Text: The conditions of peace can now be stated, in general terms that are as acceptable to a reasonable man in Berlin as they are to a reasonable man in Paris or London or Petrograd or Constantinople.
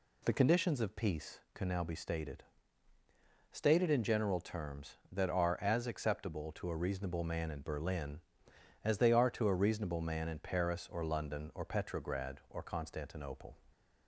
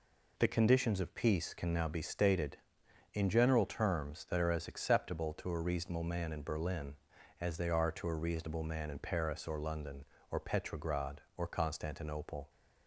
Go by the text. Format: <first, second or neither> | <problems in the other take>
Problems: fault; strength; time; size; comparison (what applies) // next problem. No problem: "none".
second | says "stated" twice; at 3.5 s